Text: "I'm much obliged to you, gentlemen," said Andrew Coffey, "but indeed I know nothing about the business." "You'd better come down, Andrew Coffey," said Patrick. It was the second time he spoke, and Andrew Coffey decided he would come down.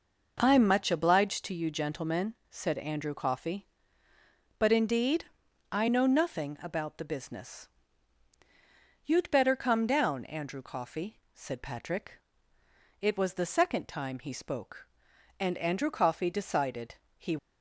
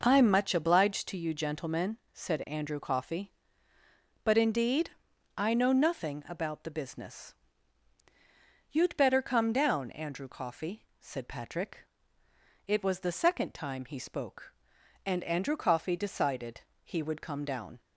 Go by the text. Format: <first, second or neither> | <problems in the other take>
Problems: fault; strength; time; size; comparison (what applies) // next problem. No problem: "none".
second | pauses between "indeed" and "I"; noticeable; at 5.2 s; 0.48 s long; noticeable in the second // pauses between "decided" and "he"; slight; at 16.9 s; 0.22 s long; slight in the second // stops before "would come down"; at 17.3 s